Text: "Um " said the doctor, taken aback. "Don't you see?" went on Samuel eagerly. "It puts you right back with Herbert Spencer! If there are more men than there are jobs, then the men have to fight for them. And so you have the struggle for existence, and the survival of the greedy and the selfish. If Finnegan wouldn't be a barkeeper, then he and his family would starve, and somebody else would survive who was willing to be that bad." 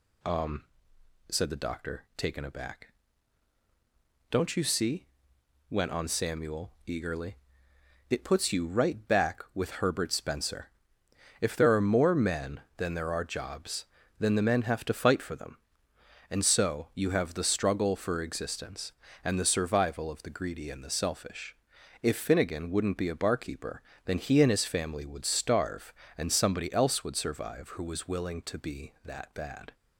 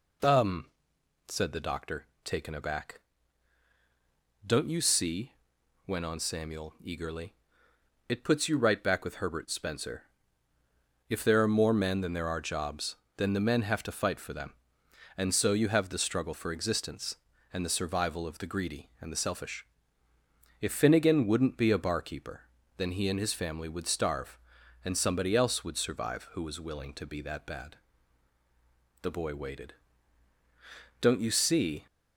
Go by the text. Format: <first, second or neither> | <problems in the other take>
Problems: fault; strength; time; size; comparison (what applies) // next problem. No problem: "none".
first | goes on to say "The boy waited Don't you see"; strong; from 29.0 s on; 2.8 s long